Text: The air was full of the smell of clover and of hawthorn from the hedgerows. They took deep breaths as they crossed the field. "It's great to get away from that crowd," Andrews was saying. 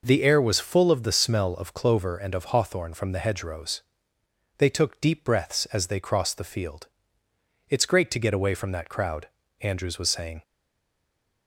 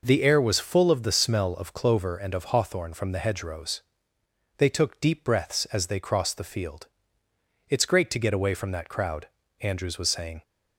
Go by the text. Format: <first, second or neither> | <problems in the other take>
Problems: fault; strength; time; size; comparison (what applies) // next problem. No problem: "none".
second | stays silent after the last word; from 10.4 s on; 1.0 s long